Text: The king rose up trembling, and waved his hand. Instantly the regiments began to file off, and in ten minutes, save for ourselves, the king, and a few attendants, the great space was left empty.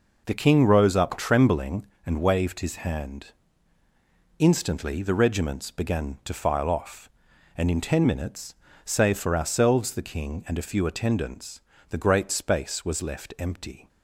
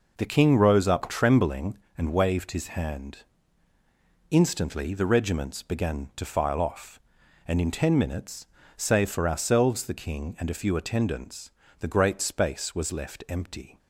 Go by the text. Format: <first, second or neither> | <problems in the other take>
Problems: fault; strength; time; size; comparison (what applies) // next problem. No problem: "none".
neither | none